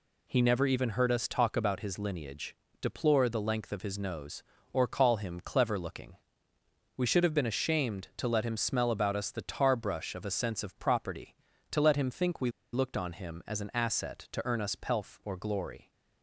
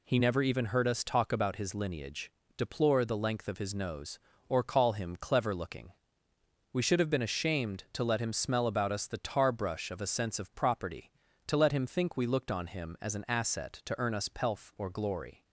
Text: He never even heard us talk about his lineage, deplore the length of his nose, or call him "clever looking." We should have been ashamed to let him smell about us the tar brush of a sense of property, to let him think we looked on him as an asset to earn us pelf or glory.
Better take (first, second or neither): second